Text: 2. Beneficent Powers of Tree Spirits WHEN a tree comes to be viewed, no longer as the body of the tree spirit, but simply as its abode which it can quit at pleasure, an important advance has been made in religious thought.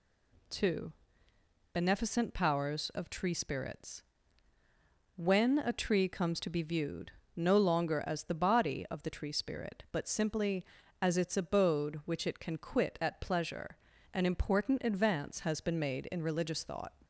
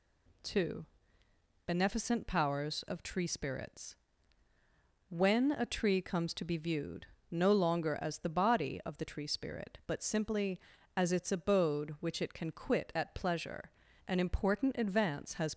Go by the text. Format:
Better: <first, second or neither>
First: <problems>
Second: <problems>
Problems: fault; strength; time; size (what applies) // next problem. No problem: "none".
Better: first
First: pauses between "Spirits" and "WHEN"; at 4.0 s; 1.1 s long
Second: pauses between "Spirits" and "WHEN"; at 3.9 s; 1.1 s long // stops before "been made in religious thought"; at 15.5 s